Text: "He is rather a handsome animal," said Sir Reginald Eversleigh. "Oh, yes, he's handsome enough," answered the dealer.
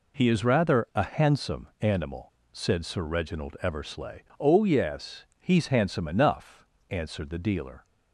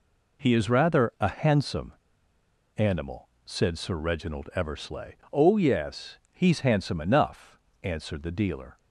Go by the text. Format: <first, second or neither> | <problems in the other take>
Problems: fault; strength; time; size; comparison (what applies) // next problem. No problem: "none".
first | pauses between "handsome" and "animal"; noticeable; at 1.9 s; 0.85 s long